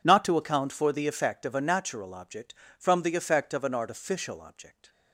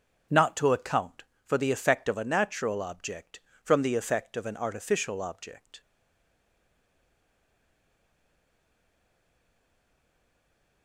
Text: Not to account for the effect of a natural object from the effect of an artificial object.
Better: first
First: none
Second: starts louder than the rest; strong; until 1.5 s; 7.5 dB // stays silent after the last word; strong; from 5.8 s on; 5.0 s long

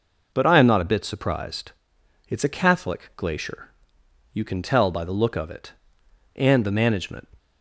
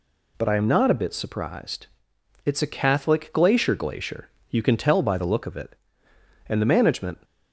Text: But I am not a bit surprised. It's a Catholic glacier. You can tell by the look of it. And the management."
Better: first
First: none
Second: says "glacier" twice; at 3.7 s

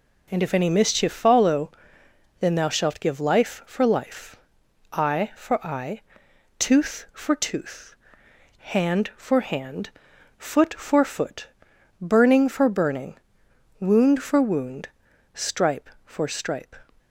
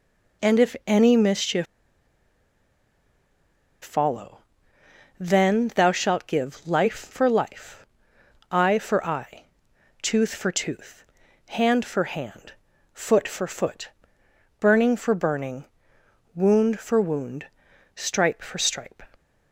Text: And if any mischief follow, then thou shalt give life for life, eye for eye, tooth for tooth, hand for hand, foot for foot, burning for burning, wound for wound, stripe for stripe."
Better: first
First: none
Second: pauses between "mischief" and "follow"; strong; at 1.6 s; 2.1 s long

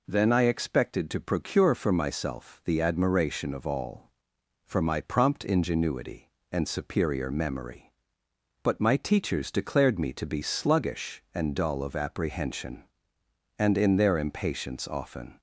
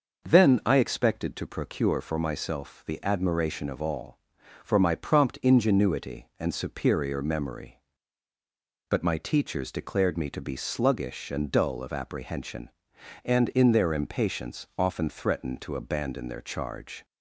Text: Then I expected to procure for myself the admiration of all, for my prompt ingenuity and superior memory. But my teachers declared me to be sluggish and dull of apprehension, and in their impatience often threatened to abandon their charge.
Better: second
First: stops before "threatened to abandon their charge"; at 15.3 s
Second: none

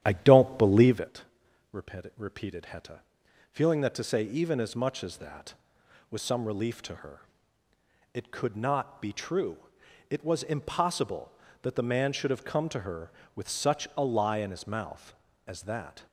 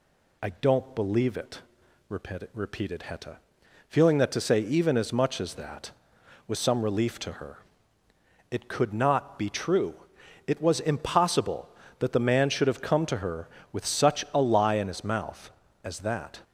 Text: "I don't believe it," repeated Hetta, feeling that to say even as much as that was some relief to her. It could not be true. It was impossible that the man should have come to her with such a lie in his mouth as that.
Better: second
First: starts louder than the rest; strong; until 1.2 s; 10.5 dB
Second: none

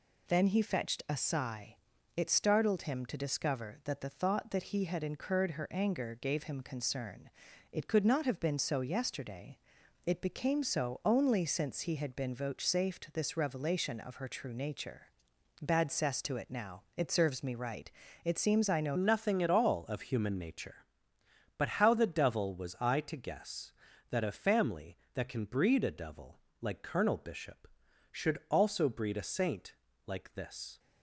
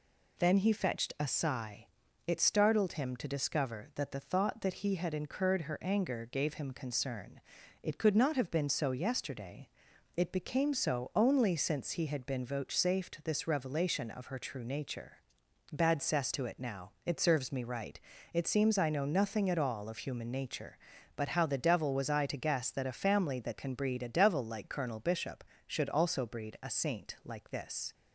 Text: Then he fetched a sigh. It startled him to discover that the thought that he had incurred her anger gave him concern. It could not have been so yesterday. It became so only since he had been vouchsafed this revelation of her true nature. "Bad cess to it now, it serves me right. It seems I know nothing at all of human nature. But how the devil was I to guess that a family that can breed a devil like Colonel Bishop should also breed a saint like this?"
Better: second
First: changes voice at "nothing"; from 18.9 s on; 11.8 s long // pauses between "devil" and "like"; slight; at 26.3 s; 0.22 s long // pauses between "saint" and "like"; slight; at 29.7 s; 0.32 s long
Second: none

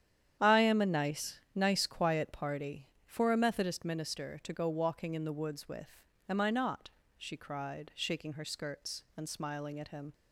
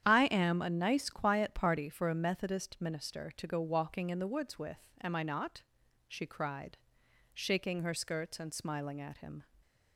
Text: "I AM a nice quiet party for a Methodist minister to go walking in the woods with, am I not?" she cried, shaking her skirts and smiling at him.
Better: second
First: starts louder than the rest; strong; until 1.5 s; 9.5 dB // says "nice" twice; at 1.5 s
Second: starts louder than the rest; strong; until 1.0 s; 9.5 dB

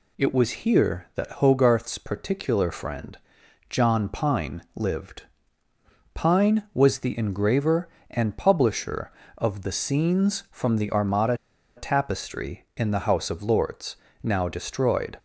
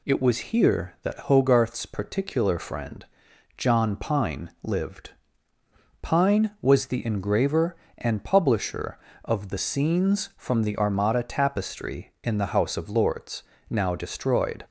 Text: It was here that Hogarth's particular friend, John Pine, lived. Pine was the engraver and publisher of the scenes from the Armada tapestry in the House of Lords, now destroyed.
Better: second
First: pauses between "Armada" and "tapestry"; at 11.3 s; 0.41 s long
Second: none

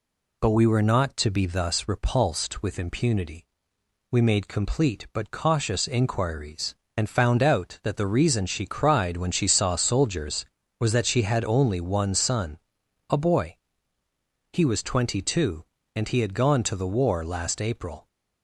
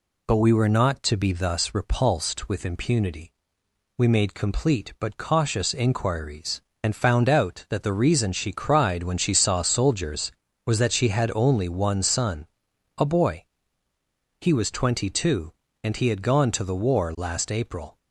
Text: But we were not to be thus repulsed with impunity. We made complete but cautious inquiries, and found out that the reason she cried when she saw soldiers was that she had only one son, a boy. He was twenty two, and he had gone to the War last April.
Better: neither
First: none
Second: none

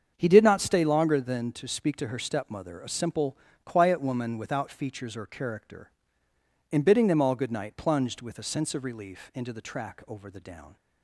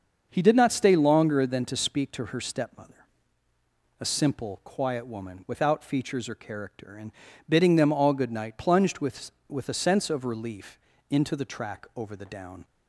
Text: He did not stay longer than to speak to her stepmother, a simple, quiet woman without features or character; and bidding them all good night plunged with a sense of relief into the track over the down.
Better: first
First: starts louder than the rest; until 1.1 s; 7 dB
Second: starts louder than the rest; until 1.3 s; 6.5 dB // pauses between "and" and "bidding"; at 7.1 s; 0.38 s long // says "with" twice; at 9.4 s // pauses between "relief" and "into"; slight; at 10.7 s; 0.32 s long

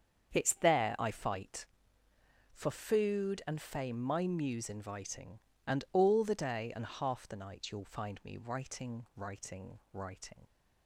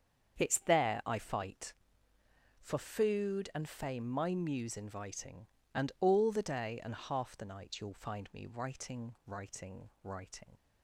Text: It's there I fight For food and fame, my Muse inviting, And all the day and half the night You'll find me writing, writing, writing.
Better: neither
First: starts louder than the rest; strong; until 1.3 s; 7.5 dB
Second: starts louder than the rest; strong; until 1.4 s; 7.5 dB

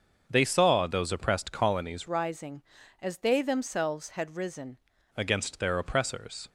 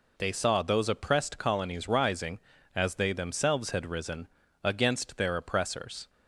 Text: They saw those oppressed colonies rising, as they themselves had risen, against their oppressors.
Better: second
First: starts louder than the rest; until 1.2 s; 6.5 dB // changes voice from "rising" to "risen"; from 2.0 to 4.7 s; 2.7 s long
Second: none

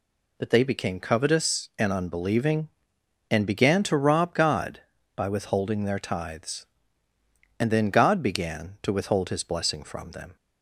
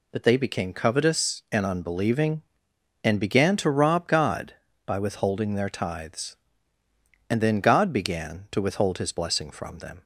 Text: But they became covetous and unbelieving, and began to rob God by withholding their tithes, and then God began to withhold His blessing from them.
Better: neither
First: none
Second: none

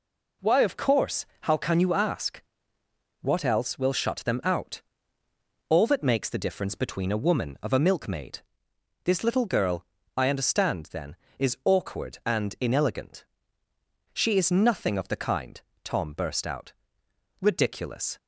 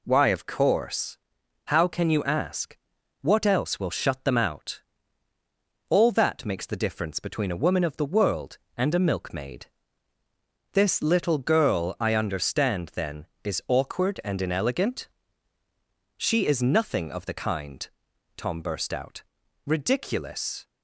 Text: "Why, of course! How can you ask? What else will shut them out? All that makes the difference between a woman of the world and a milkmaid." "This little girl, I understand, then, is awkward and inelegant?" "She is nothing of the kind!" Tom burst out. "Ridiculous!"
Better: second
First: skips "the world and"; at 7.7 s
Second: none

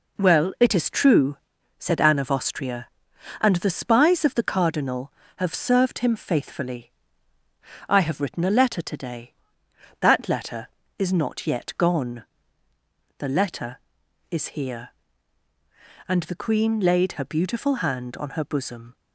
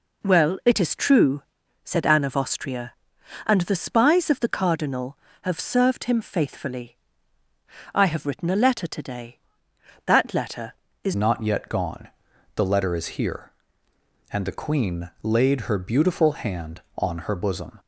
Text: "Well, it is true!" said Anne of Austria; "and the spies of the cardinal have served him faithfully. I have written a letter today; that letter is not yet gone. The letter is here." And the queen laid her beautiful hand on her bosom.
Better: first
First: none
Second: changes voice at "not"; from 11.1 s on; 6.6 s long

